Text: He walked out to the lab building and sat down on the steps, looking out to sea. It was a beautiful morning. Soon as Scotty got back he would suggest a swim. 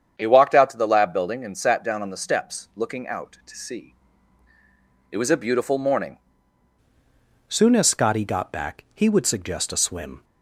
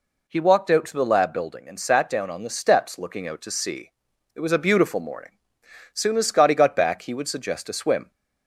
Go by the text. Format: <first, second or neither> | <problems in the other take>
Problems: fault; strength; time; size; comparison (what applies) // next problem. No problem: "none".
second | starts louder than the rest; strong; until 1.2 s; 8 dB // changes voice at "Soon"; from 7.4 s on; 2.8 s long